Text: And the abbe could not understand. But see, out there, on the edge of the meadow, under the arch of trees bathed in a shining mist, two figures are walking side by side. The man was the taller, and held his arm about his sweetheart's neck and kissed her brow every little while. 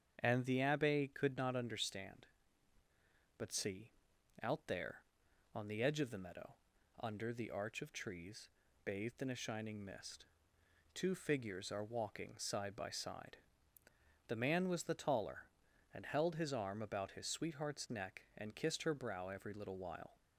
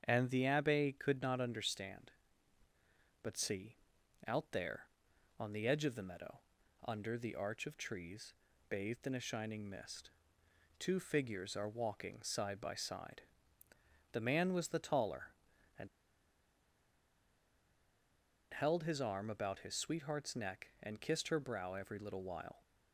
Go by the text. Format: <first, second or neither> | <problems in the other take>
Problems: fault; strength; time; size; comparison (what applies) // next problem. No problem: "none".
first | starts louder than the rest; strong; until 1.0 s; 7.5 dB; strong in the first // pauses between "trees" and "bathed"; slight; at 8.3 s; 0.36 s long; slight in the first // pauses between "and" and "held"; strong; at 15.8 s; 2.6 s long